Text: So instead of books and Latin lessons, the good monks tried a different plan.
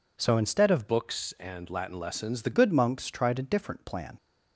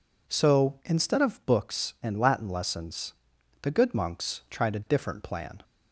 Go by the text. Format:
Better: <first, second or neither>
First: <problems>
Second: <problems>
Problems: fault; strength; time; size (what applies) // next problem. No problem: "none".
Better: second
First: changes voice from "books" to "the"; from 0.8 to 2.5 s; 1.7 s long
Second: none